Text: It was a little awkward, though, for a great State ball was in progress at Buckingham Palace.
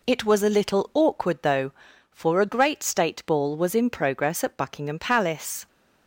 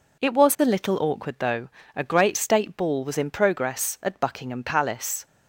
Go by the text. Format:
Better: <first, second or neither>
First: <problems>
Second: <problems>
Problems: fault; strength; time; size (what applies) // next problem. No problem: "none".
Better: first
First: none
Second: skips "for"; at 1.8 s